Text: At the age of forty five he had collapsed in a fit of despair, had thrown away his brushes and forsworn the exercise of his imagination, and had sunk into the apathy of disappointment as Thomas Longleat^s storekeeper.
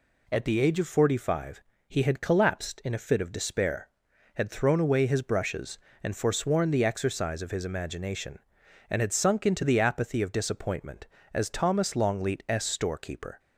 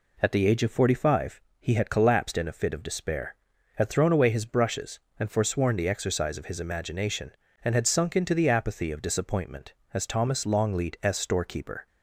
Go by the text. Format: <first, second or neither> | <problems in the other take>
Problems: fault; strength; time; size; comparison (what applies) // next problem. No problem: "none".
neither | pauses between "five" and "he"; slight; the same in both